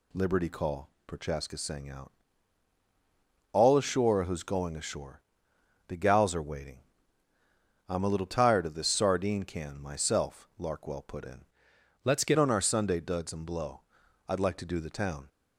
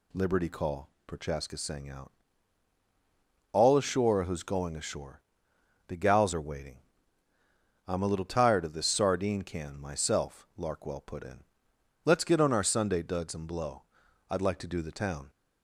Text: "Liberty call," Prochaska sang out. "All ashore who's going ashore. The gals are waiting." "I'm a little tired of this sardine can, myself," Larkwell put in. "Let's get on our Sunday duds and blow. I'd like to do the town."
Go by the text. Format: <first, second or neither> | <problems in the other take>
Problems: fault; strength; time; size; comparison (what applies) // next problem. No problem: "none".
second | changes voice from "Let's" to "get"; from 12.0 to 12.3 s; 0.3 s long